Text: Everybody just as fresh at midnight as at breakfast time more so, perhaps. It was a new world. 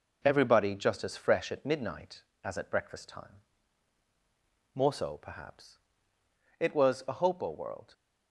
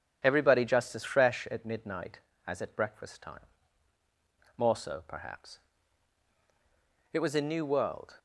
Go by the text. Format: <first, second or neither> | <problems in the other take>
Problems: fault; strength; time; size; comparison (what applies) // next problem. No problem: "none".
second | pauses between "time" and "more"; strong; at 3.4 s; 1.3 s long; also in the second // says "hopo" for "new"; at 7.1 s